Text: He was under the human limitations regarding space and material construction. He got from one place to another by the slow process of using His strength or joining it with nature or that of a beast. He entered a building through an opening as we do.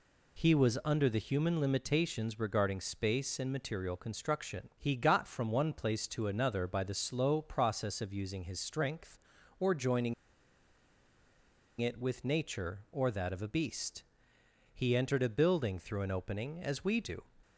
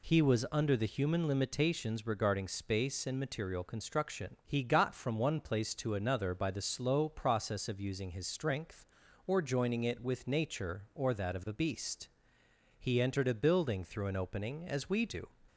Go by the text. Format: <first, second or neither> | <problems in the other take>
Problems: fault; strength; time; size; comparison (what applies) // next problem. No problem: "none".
second | pauses between "joining" and "it"; strong; at 10.1 s; 1.6 s long